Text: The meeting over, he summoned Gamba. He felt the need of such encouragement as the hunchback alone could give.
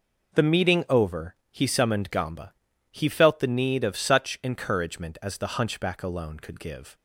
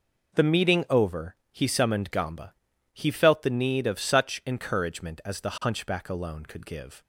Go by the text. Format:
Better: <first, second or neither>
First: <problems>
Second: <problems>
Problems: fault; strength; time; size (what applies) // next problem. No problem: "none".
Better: neither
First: none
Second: none